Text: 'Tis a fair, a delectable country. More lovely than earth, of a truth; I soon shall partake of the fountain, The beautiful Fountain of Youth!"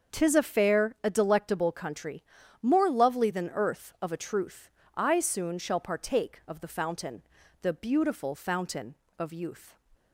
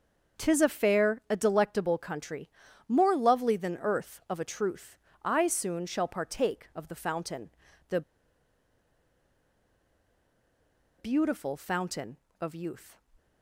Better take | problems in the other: first | starts louder than the rest; until 1.4 s; 6 dB; also in the first // pauses between "The" and "beautiful"; strong; at 8.0 s; 2.9 s long

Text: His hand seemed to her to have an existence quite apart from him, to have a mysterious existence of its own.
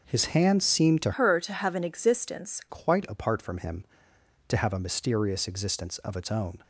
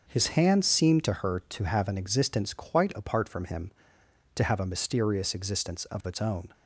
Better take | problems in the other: second | changes voice from "her" to "existence"; from 1.1 to 2.6 s; 1.5 s long

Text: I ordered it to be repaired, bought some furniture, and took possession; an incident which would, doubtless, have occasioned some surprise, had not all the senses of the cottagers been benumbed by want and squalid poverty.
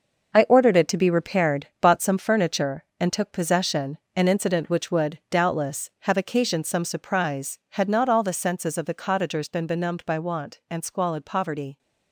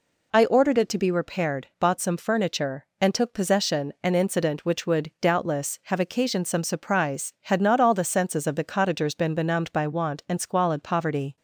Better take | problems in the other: second | gets quieter; strong; throughout; 9 dB

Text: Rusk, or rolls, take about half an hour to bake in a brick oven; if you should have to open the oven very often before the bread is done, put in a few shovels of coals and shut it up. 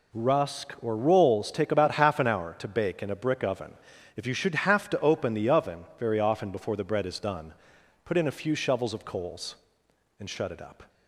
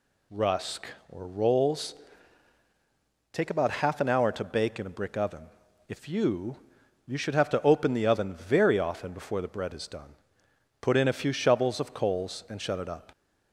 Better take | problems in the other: first | says "you" twice; at 7.0 s

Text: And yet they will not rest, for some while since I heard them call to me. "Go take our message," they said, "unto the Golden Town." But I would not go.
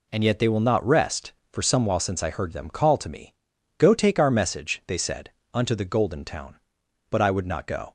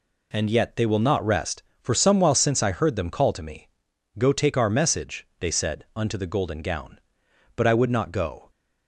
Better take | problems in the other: first | says "Gown" for "Town"; at 6.6 s

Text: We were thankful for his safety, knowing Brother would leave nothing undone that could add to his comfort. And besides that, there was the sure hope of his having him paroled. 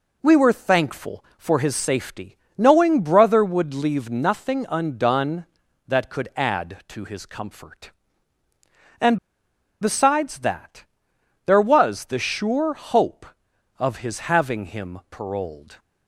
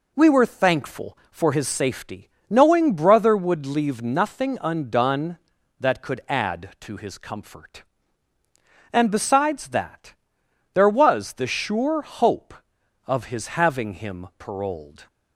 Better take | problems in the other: second | pauses between "And" and "besides"; noticeable; at 9.1 s; 0.63 s long

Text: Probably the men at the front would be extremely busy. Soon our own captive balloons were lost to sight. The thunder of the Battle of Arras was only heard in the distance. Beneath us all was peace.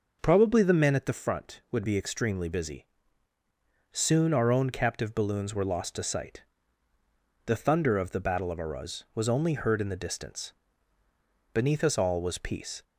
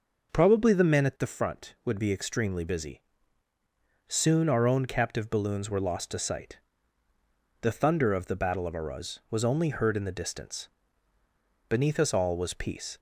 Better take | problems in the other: neither | none

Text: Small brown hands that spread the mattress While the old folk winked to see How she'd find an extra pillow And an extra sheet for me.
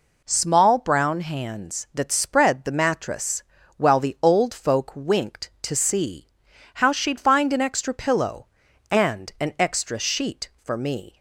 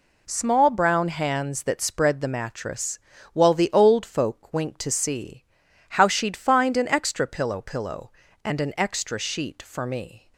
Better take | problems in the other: first | pauses between "mattress" and "While"; slight; at 2.9 s; 0.34 s long; slight in the first // pauses between "see" and "How"; noticeable; at 5.4 s; 0.46 s long; noticeable in the first // says "pillow" twice; at 7.6 s

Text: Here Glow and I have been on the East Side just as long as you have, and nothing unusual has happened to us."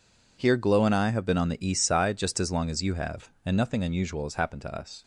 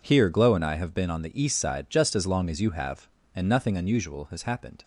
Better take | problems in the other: first | stops before "to us"; at 4.8 s

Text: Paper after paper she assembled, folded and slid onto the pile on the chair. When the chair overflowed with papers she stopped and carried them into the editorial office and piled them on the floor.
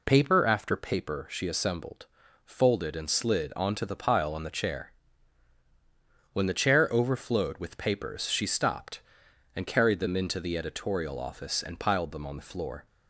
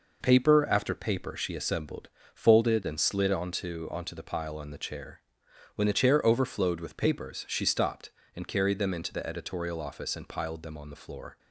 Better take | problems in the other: first | says "onto" twice; at 3.9 s

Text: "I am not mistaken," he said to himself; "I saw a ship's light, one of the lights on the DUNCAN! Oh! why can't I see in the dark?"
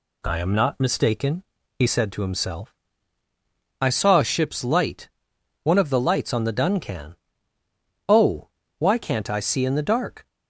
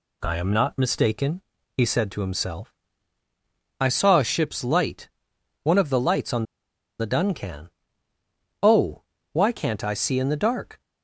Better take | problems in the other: first | pauses between "on" and "the"; noticeable; at 6.4 s; 0.55 s long

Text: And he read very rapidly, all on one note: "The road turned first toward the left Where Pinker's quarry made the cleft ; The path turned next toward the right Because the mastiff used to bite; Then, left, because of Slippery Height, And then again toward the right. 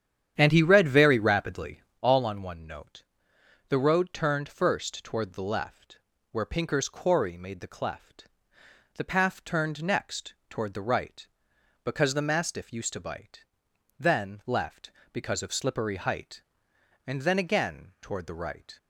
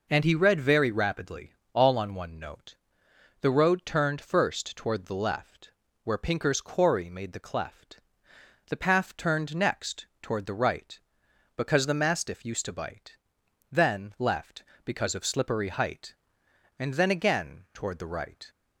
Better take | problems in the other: second | starts louder than the rest; strong; until 2.0 s; 9.5 dB // pauses between "left" and "Where"; slight; at 5.9 s; 0.34 s long; slight in the second // pauses between "next" and "toward"; slight; at 10.3 s; 0.16 s long; slight in the second

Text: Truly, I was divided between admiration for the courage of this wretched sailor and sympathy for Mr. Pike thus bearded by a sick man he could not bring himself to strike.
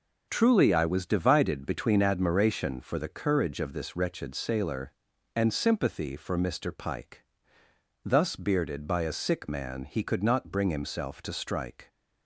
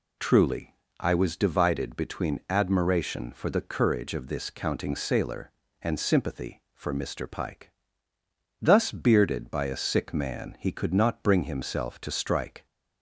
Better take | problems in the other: first | says "counting" for "wretched"; at 4.4 s // pauses between "Pike" and "thus"; noticeable; at 7.6 s; 0.90 s long; noticeable in the first

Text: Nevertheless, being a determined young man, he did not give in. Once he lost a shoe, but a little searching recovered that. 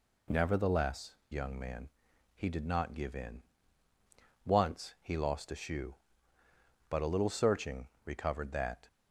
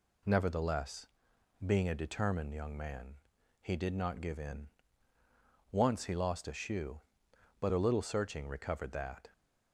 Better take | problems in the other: second | skips "being a determined"; at 1.2 s // pauses between "searching" and "recovered"; slight; at 7.8 s; 0.16 s long

